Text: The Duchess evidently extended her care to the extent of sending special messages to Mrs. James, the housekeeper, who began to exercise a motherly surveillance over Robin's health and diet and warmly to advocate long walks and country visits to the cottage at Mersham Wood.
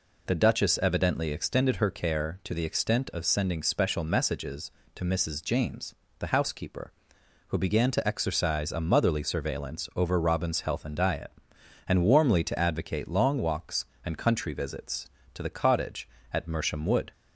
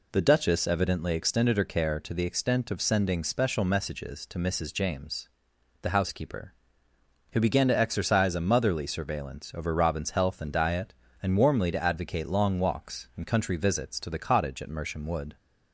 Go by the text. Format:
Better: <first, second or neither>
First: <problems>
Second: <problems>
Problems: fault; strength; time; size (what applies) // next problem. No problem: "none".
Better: neither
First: none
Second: none